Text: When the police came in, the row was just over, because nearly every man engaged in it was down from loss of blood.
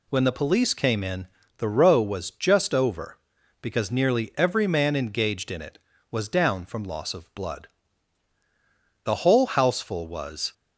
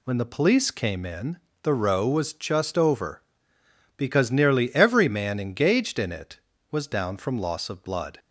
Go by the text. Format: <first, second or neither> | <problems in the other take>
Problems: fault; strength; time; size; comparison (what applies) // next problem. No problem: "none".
second | goes on to say "The whole houseful was"; from 9.0 s on; 1.4 s long